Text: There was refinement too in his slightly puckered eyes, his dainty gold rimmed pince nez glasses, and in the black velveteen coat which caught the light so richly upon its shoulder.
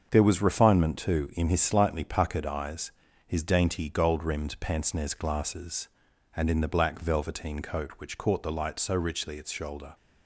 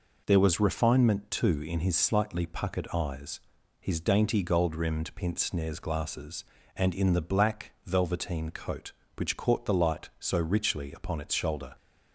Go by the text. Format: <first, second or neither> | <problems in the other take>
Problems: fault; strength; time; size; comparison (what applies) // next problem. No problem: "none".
second | starts louder than the rest; until 1.1 s; 6.5 dB // skips "upon"; at 9.3 s